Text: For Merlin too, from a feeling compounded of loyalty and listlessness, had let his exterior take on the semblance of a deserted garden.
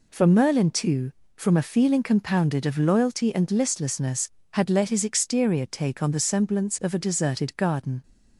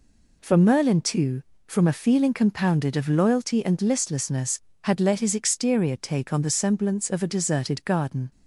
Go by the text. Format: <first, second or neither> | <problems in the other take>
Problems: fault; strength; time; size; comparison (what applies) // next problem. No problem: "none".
neither | none